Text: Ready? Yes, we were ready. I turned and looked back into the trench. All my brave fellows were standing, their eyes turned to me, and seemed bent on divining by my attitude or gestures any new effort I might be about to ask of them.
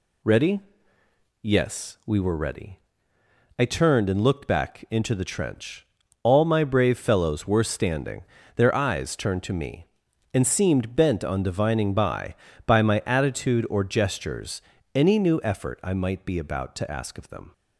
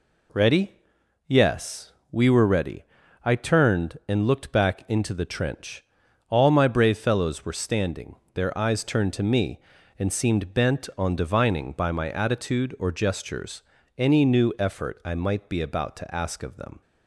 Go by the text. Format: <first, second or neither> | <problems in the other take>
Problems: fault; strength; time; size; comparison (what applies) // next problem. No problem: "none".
second | says "by" twice; at 12.6 s // pauses between "gestures" and "any"; slight; at 14.6 s; 0.34 s long; slight in the second